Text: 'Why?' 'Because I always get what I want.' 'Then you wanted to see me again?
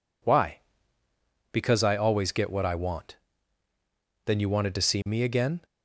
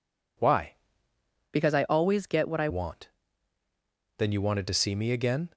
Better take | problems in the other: first | changes voice from "Because" to "I"; from 1.5 to 2.6 s; 1.1 s long

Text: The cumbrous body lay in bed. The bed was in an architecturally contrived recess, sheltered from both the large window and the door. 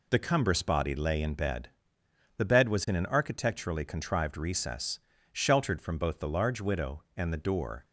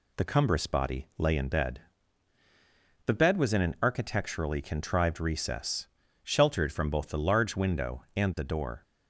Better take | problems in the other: second | says "widow" for "window"; at 6.6 s

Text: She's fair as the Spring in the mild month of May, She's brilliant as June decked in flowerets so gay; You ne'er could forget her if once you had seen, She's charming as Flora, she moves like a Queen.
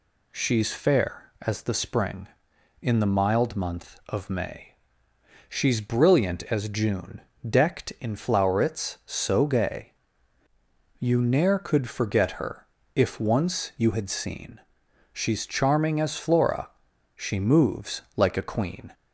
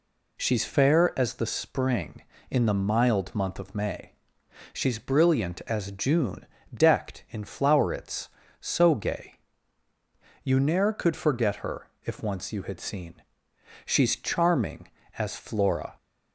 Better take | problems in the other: first | pauses between "June" and "decked"; slight; at 6.4 s; 0.28 s long; slight in the first // pauses between "her" and "if"; slight; at 11.8 s; 0.16 s long; slight in the first // stops before "she moves like a Queen"; at 15.9 s

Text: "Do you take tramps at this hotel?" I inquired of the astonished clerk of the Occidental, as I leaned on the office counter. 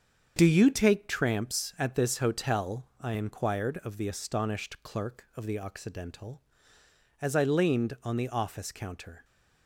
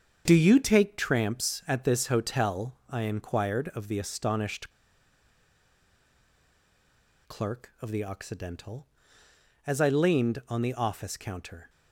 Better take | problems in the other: first | starts louder than the rest; strong; until 1.2 s; 7.5 dB; strong in the first // pauses between "astonished" and "clerk"; strong; at 4.7 s; 2.5 s long

